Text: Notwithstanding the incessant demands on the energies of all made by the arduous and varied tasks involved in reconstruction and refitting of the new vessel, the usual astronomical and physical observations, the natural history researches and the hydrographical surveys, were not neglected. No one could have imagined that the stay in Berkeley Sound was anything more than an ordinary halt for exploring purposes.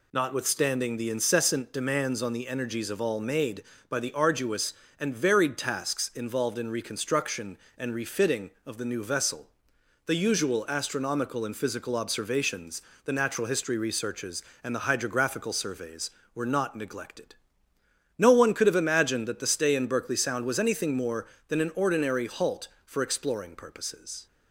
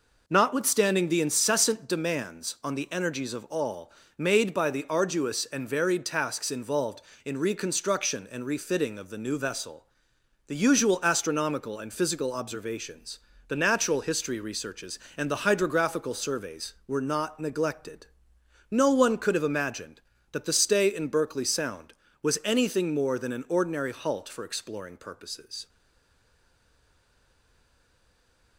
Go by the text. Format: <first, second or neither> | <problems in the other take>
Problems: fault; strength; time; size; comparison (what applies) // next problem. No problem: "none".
first | pauses between "all" and "made"; slight; at 3.9 s; 0.26 s long // stays silent after the last word; strong; from 25.6 s on; 2.9 s long